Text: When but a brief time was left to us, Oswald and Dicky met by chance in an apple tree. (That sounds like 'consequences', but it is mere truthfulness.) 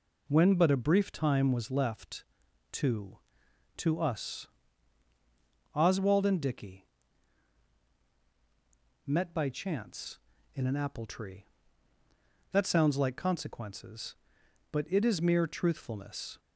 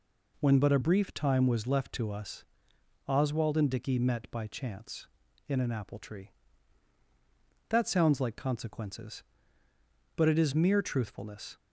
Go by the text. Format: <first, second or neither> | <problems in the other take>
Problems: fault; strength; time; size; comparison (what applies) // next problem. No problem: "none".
second | says "to" twice; at 3.7 s // pauses between "Dicky" and "met"; strong; at 6.8 s; 2.2 s long